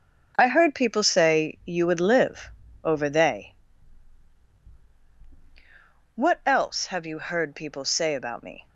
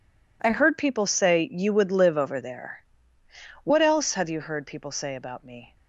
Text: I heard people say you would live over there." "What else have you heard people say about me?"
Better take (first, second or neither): second